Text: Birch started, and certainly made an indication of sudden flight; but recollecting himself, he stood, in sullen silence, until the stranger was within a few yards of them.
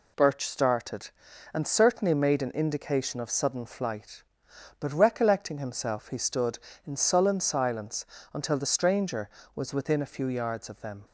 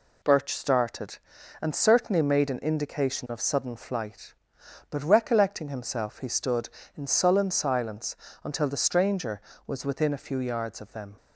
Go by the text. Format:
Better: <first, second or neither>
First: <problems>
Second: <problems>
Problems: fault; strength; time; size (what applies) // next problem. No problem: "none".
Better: neither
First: none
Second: none